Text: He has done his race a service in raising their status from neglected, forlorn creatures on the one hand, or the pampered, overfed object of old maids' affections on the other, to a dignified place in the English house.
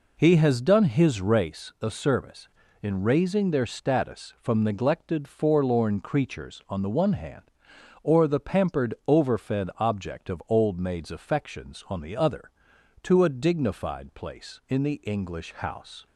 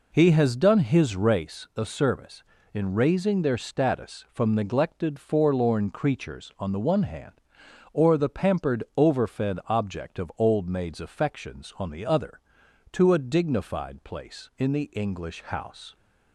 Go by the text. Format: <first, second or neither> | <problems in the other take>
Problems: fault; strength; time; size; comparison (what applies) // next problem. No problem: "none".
neither | none